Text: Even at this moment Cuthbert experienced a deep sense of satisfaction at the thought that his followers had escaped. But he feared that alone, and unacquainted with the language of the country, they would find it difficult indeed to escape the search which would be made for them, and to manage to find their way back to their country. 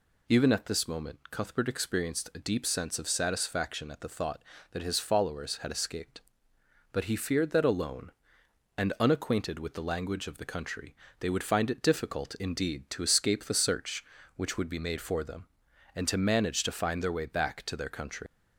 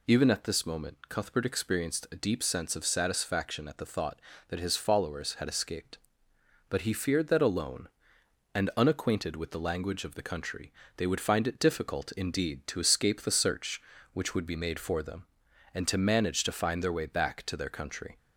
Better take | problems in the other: second | leaves "country" unfinished; at 18.2 s; 105 ms

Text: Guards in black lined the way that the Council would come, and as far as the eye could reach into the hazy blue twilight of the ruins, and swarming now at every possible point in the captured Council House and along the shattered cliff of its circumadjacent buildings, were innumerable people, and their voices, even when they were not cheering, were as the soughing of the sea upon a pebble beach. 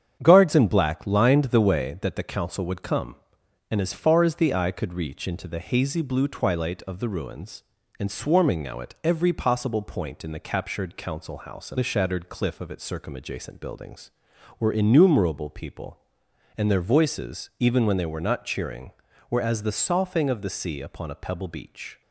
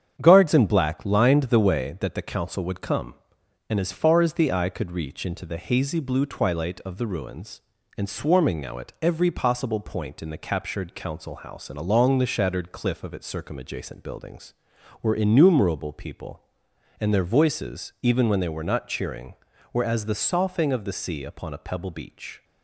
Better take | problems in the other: second | starts louder than the rest; strong; until 1.2 s; 8 dB; strong in the second // skips "along"; at 11.7 s

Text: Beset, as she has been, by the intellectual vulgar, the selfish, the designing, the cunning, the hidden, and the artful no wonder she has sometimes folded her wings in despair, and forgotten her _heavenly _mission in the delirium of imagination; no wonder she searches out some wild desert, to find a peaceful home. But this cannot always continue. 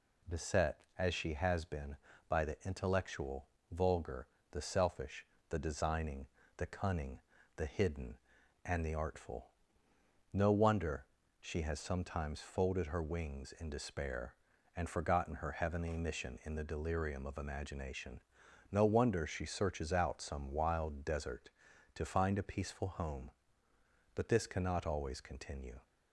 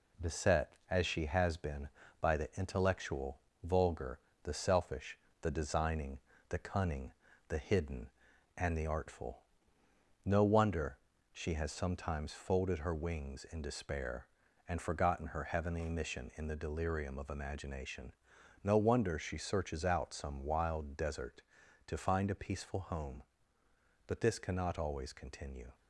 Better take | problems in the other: first | gets quieter; throughout; 3.5 dB // pauses between "intellectual" and "vulgar"; slight; at 3.3 s; 0.24 s long; slight in the first // pauses between "artful" and "no"; noticeable; at 9.4 s; 0.82 s long; noticeable in the first // pauses between "wonder" and "she"; at 10.9 s; 0.38 s long; also in the first

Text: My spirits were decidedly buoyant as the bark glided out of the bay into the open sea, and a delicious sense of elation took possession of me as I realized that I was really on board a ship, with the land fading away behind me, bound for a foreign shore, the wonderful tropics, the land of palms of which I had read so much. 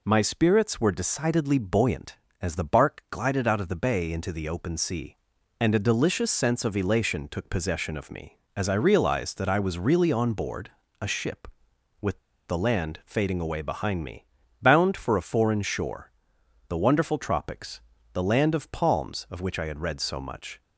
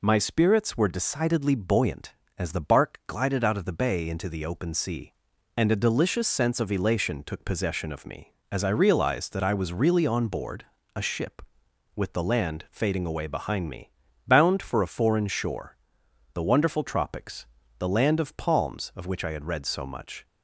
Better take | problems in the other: second | pauses between "board" and "a"; slight; at 10.6 s; 0.32 s long; slight in the second // pauses between "with" and "the"; slight; at 12.1 s; 0.30 s long

